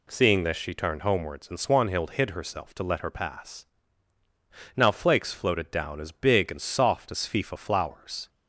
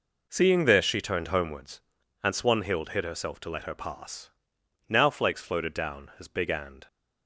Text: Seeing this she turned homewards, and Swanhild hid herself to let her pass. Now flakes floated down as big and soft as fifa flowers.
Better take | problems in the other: first | stops before "soft as fifa flowers"; at 6.8 s

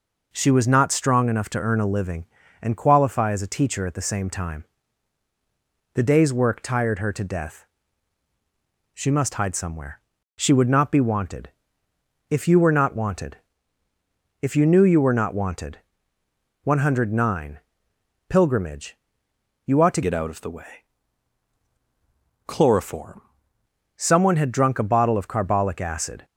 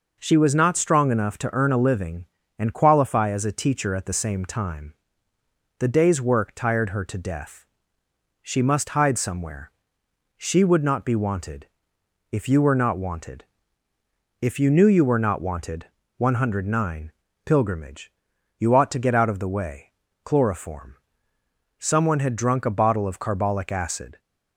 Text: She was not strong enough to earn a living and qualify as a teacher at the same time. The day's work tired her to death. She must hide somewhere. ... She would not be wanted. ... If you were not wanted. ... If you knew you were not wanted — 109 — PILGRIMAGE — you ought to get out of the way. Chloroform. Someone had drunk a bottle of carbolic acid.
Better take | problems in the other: second | changes voice from "get" to "Chloroform"; from 20.0 to 23.2 s; 3.2 s long

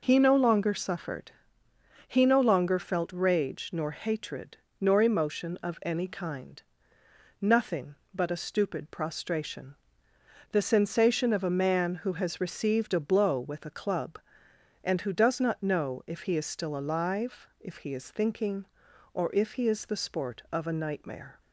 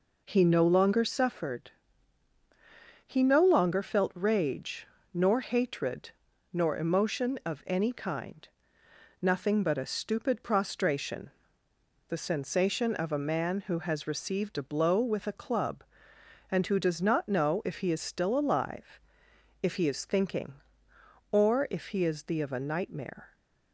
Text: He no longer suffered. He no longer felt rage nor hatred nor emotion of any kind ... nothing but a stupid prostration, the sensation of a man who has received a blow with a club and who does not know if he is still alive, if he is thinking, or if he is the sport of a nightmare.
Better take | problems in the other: first | pauses between "rage" and "nor"; slight; at 4.8 s; 0.26 s long // pauses between "hatred" and "nor"; at 6.1 s; 0.40 s long; slight in the first // skips "sport"; at 22.4 s

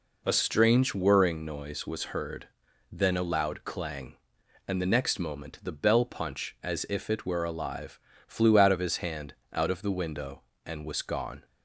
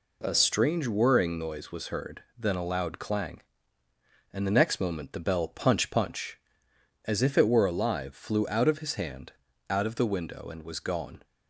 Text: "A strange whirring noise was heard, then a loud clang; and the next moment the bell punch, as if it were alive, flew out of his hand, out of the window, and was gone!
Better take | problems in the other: first | says "punch" twice; at 5.8 s

